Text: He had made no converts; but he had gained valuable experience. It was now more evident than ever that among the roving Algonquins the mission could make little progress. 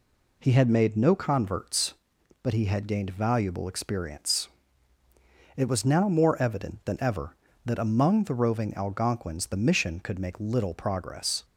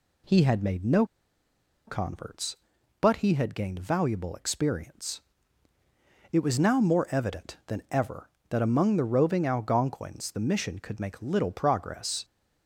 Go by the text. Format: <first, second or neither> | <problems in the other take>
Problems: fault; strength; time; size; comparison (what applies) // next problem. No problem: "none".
first | pauses between "no" and "converts"; noticeable; at 1.0 s; 0.82 s long